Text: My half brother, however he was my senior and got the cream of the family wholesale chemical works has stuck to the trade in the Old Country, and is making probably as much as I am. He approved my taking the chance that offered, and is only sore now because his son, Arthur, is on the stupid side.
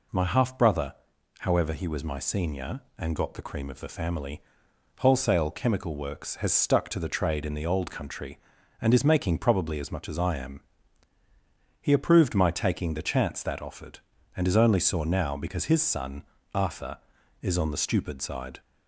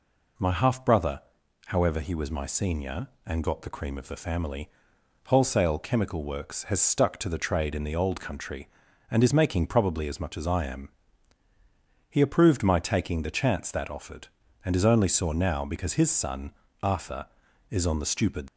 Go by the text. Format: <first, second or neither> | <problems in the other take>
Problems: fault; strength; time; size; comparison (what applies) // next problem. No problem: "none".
first | pauses between "family" and "wholesale"; noticeable; at 4.6 s; 0.58 s long; noticeable in the first // stops before "side"; at 18.4 s